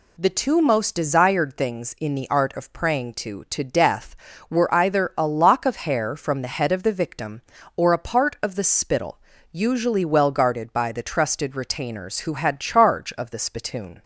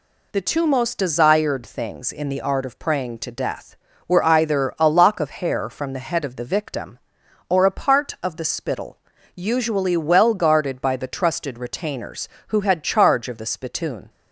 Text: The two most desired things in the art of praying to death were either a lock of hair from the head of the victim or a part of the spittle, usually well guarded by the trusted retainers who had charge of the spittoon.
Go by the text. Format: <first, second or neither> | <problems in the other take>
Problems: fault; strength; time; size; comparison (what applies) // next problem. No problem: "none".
second | says "to" twice; at 3.4 s